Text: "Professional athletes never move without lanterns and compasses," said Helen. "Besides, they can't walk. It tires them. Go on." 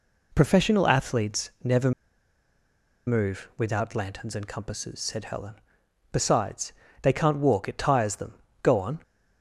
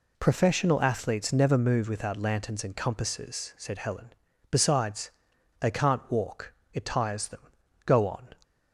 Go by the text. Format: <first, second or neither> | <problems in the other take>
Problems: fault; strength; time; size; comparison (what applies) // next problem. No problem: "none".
second | pauses between "never" and "move"; at 1.9 s; 1.1 s long